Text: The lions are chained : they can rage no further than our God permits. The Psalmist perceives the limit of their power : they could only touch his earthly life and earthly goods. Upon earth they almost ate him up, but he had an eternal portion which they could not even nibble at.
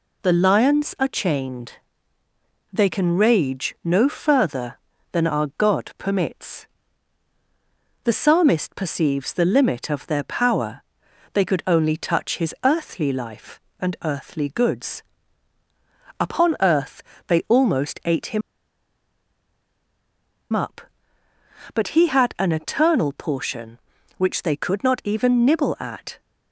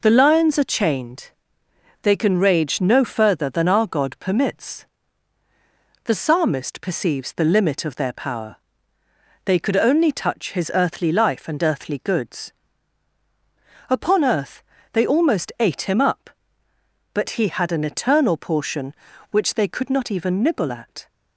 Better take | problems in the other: second | pauses between "earth" and "they"; slight; at 17.0 s; 0.26 s long; slight in the second // pauses between "him" and "up"; strong; at 18.4 s; 2.1 s long

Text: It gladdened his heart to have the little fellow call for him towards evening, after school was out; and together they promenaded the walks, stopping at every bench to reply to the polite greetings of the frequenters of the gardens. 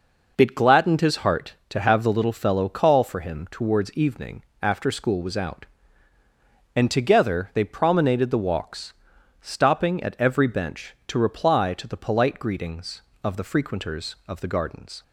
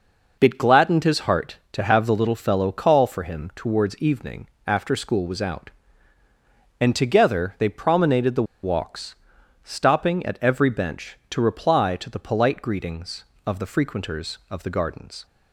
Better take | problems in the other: first | pauses between "the" and "walks"; slight; at 8.4 s; 0.19 s long

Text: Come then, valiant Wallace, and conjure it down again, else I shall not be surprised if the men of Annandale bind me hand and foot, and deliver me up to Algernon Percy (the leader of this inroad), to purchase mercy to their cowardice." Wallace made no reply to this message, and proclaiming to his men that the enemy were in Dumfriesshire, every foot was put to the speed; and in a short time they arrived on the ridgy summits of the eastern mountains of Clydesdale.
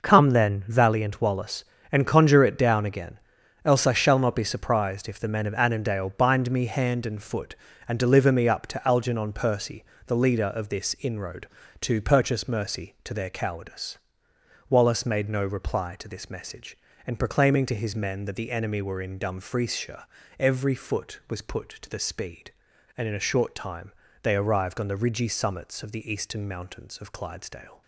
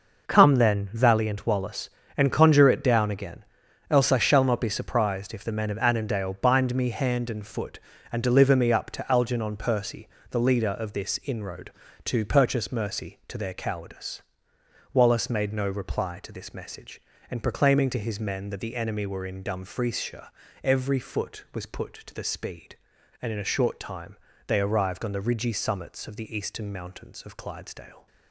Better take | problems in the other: neither | pauses between "time" and "they"; slight; the same in both

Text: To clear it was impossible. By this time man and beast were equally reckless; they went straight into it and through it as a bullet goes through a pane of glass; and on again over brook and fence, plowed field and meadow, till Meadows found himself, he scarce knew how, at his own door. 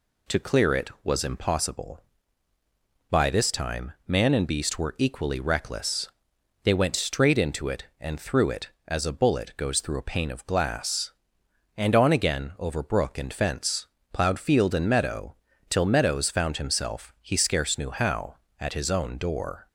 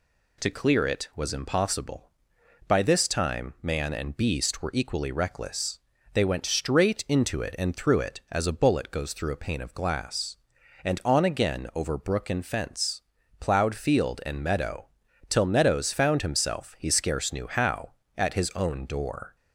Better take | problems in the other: neither | none

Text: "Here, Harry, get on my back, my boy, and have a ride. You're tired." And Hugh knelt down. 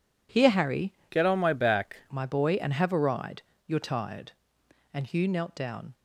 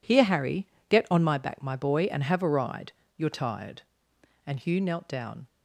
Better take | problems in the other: second | changes voice from "get" to "back"; from 1.0 to 1.9 s; 0.9 s long

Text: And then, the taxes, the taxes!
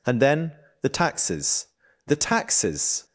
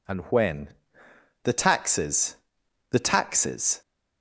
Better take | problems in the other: first | says "when" for "then"; at 0.2 s

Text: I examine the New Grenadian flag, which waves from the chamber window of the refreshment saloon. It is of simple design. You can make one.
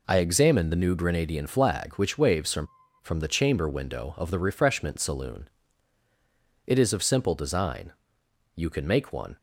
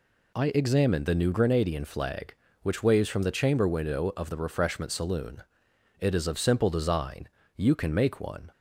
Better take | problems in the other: second | says "from" twice; at 3.0 s

